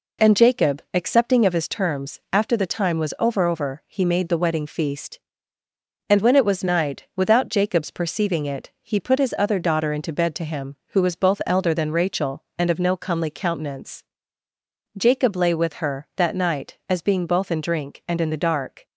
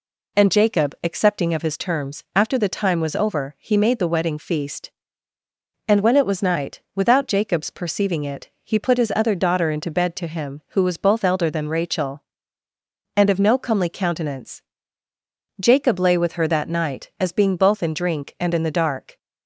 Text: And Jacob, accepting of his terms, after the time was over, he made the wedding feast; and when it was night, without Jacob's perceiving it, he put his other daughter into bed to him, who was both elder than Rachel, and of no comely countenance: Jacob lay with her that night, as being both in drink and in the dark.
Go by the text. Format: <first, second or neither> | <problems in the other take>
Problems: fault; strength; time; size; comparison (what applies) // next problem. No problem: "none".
second | says "over" twice; at 3.4 s